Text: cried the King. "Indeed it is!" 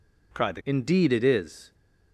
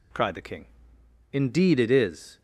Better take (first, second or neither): second